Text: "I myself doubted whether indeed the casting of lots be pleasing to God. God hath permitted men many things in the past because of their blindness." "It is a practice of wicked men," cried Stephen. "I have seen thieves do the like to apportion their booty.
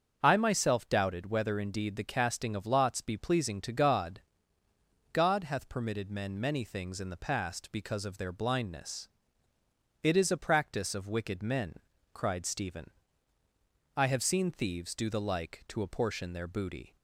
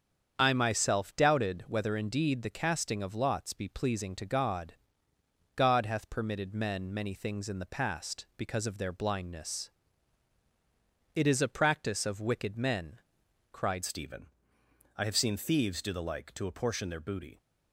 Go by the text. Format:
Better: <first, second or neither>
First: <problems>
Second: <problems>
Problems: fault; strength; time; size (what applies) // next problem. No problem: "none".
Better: first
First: starts louder than the rest; until 1.2 s; 6.5 dB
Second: starts louder than the rest; strong; until 1.4 s; 7.5 dB // changes voice at "Stephen"; from 13.8 s on; 3.5 s long